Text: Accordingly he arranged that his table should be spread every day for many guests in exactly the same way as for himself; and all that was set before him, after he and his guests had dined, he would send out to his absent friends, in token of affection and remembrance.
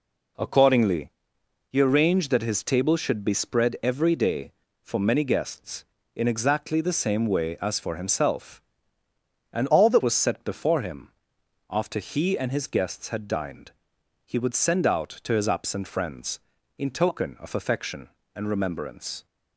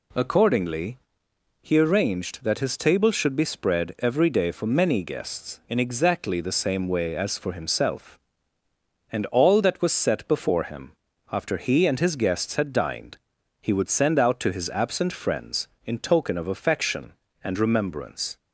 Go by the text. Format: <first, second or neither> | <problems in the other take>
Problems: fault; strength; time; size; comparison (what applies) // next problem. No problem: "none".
second | pauses between "Accordingly" and "he"; noticeable; at 1.1 s; 0.58 s long; noticeable in the second // changes voice from "all" to "that"; from 9.7 to 10.0 s; 0.3 s long